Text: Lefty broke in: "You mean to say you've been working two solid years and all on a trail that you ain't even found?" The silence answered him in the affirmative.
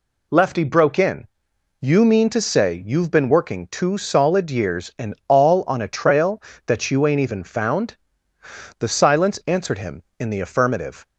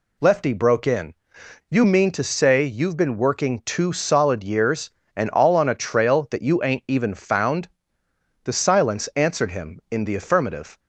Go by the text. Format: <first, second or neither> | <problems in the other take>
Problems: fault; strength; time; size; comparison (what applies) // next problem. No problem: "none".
neither | none